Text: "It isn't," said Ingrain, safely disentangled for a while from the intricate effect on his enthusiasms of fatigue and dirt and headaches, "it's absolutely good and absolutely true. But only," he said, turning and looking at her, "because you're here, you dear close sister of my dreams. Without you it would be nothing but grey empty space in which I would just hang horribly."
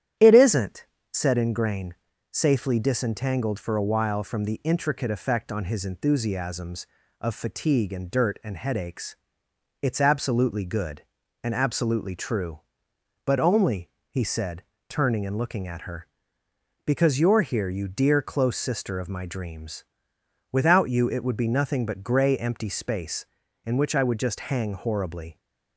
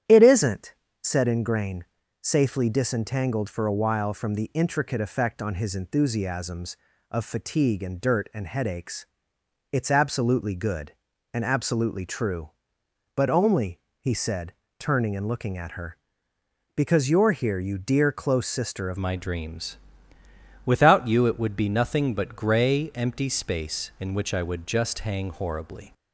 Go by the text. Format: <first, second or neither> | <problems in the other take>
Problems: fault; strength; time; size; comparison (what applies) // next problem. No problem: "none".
first | starts louder than the rest; strong; until 1.3 s; 10.5 dB; strong in the first // changes voice at "my"; from 18.9 s on; 7.0 s long